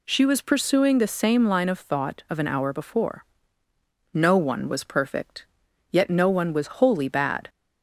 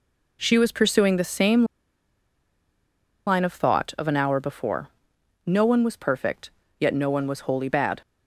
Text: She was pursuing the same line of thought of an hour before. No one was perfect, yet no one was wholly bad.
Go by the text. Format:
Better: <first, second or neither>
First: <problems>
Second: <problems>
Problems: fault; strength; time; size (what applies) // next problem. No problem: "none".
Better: first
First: none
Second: pauses between "same" and "line"; strong; at 1.6 s; 1.6 s long